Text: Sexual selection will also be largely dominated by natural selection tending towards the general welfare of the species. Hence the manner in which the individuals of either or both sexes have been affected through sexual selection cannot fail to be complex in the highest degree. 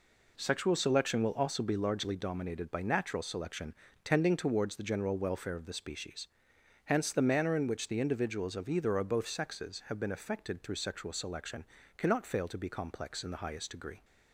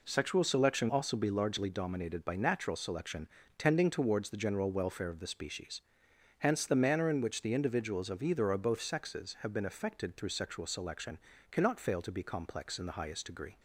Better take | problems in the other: first | skips "will"; at 0.8 s // pauses between "selection" and "tending"; slight; at 3.2 s; 0.30 s long; slight in the first // pauses between "selection" and "cannot"; slight; at 11.1 s; 0.32 s long; slight in the first

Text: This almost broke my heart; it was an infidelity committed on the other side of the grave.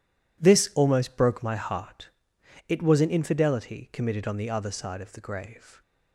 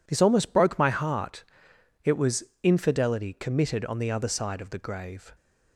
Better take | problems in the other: first | skips "an"; at 2.5 s

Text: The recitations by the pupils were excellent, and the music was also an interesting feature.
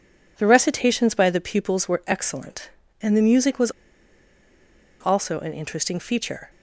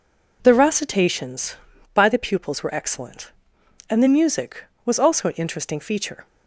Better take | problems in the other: second | pauses between "was" and "also"; strong; at 3.6 s; 1.3 s long

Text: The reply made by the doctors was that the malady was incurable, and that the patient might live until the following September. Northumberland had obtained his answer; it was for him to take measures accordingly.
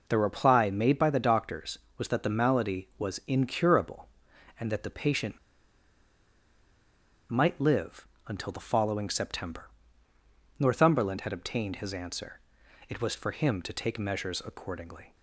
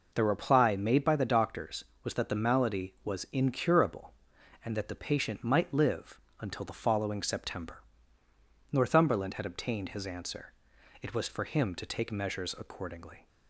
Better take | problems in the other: second | pauses between "patient" and "might"; strong; at 5.3 s; 1.9 s long // pauses between "live" and "until"; slight; at 8.0 s; 0.22 s long; slight in the second

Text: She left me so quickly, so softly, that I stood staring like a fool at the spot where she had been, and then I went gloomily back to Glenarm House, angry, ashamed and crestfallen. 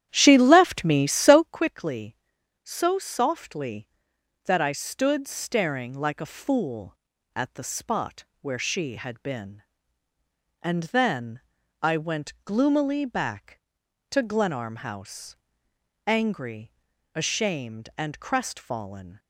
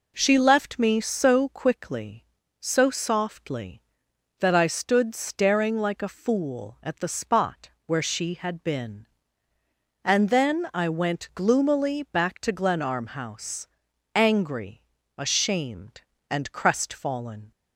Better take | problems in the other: second | starts louder than the rest; strong; until 1.5 s; 11 dB // pauses between "spot" and "where"; slight; at 8.2 s; 0.16 s long; slight in the second // pauses between "then" and "I"; at 11.4 s; 0.42 s long

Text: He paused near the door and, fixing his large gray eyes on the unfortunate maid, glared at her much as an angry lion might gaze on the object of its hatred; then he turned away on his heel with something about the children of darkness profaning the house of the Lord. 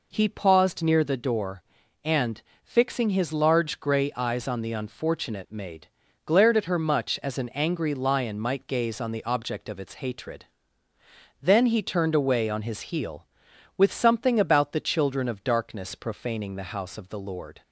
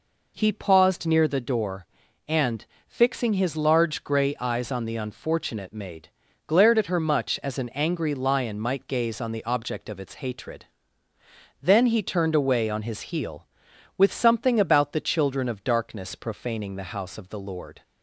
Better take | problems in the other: neither | none

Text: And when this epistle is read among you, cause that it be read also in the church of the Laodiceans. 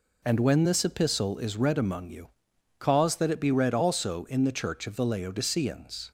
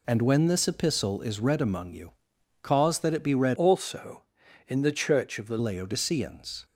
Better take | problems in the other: first | changes voice from "also" to "the"; from 3.5 to 5.5 s; 2.0 s long

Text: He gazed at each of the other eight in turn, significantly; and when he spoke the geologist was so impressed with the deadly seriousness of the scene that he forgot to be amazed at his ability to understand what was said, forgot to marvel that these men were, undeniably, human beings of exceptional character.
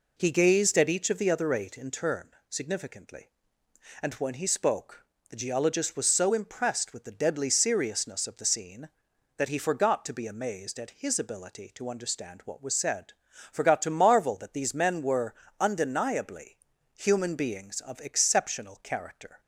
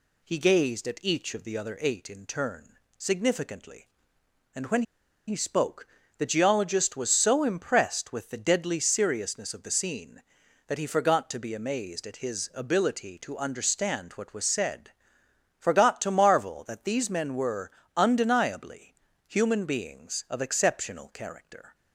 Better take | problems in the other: first | pauses between "when" and "he"; at 4.8 s; 0.45 s long // pauses between "spoke" and "the"; slight; at 5.8 s; 0.30 s long; slight in the first

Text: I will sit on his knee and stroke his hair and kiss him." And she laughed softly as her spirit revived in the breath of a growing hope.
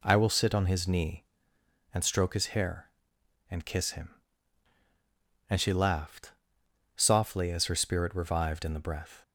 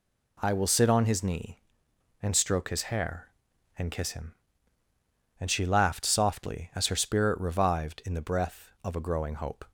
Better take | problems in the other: second | pauses between "laughed" and "softly"; noticeable; at 6.3 s; 0.64 s long // stops before "of a growing hope"; at 9.2 s

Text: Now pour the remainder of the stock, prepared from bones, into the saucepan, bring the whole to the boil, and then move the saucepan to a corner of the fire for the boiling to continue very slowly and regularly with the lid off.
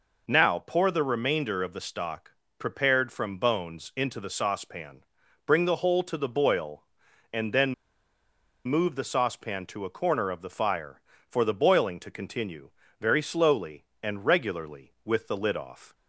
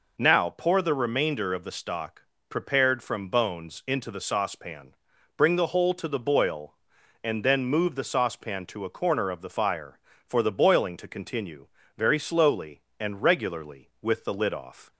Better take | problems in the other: second | pauses between "then" and "move"; noticeable; at 7.7 s; 0.92 s long // pauses between "continue" and "very"; slight; at 12.6 s; 0.32 s long; slight in the second

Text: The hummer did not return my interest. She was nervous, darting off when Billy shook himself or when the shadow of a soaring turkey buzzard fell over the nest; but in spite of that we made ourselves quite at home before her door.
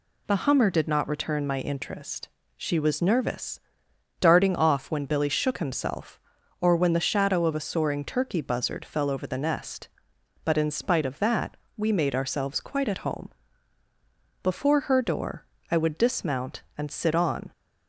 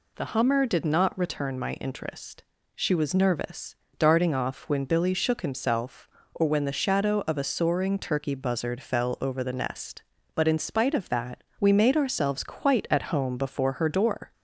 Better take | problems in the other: second | pauses between "that" and "we"; slight; at 11.5 s; 0.18 s long; slight in the second // pauses between "home" and "before"; at 13.3 s; 1.1 s long // goes on to say "I would dismount and sit on"; strong; from 15.6 s on; 1.8 s long

